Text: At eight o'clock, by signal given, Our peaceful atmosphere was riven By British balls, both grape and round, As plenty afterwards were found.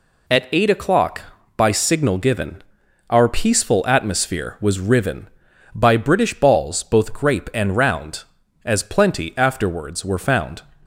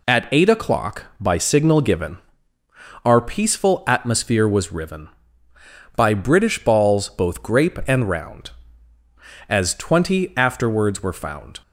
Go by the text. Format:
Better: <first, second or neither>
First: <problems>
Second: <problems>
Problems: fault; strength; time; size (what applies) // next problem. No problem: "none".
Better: first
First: none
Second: says "twenty" for "plenty"; at 9.7 s